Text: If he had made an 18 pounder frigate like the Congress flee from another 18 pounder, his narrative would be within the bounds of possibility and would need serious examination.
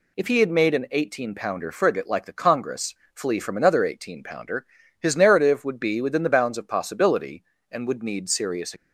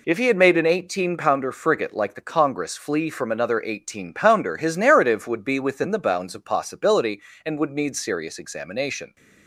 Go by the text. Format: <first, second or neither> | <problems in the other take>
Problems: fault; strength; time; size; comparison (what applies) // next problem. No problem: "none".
second | pauses between "Congress" and "flee"; slight; at 2.9 s; 0.20 s long // stops before "examination"; at 8.7 s